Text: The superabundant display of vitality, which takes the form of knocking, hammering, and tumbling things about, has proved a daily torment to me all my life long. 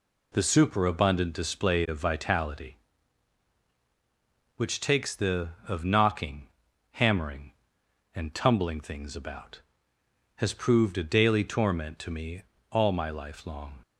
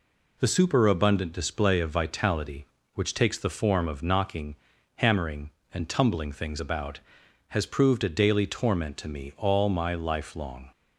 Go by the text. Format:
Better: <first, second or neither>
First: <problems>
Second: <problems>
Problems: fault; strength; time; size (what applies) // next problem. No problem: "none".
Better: second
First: skips "form"; at 5.5 s // pauses between "me" and "all"; slight; at 12.4 s; 0.30 s long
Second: none